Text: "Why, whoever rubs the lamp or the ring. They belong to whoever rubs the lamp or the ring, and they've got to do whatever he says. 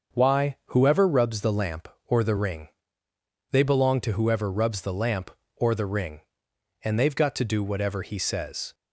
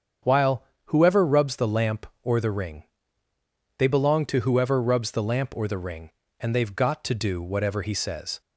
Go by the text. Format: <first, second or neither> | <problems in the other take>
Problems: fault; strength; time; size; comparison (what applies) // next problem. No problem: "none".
first | starts louder than the rest; strong; until 1.4 s; 7.5 dB; also in the first // says "While" for "Why"; at 0.2 s